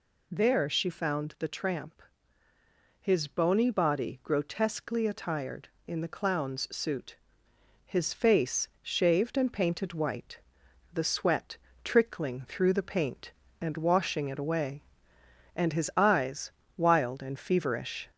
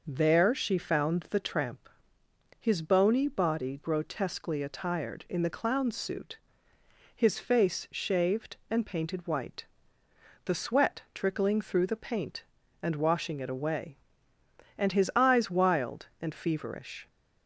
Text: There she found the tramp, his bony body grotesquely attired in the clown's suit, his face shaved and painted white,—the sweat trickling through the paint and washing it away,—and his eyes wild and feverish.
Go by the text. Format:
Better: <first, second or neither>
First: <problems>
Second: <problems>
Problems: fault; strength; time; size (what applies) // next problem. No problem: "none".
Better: second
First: gets louder; slight; throughout; 2.5 dB // pauses between "sweat" and "trickling"; slight; at 11.5 s; 0.26 s long // pauses between "eyes" and "wild"; slight; at 16.5 s; 0.26 s long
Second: none